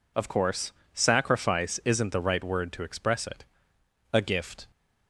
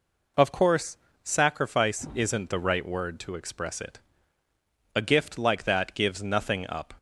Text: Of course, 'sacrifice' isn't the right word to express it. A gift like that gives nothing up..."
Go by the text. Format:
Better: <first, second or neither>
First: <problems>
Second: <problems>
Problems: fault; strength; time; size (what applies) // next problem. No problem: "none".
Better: second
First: stops before "like that gives nothing up"; at 4.7 s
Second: none